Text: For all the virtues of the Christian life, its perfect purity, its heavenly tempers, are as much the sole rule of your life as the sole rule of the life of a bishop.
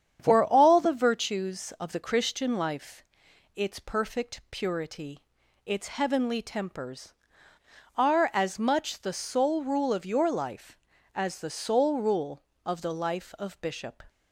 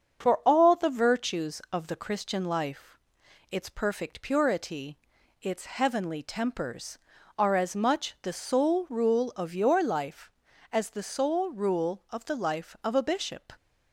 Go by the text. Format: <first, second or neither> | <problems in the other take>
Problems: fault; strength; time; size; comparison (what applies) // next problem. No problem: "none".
second | starts louder than the rest; strong; until 1.2 s; 8.5 dB; also in the second // skips "a"; at 13.6 s